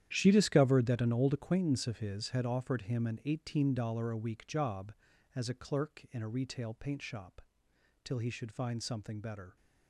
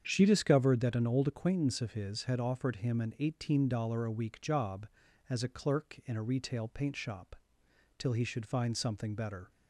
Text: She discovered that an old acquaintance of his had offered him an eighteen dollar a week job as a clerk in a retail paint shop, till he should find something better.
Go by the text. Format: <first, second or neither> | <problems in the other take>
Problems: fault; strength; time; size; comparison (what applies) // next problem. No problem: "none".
second | gets quieter; strong; throughout; 14 dB // starts louder than the rest; strong; until 1.1 s; 10.5 dB; strong in the second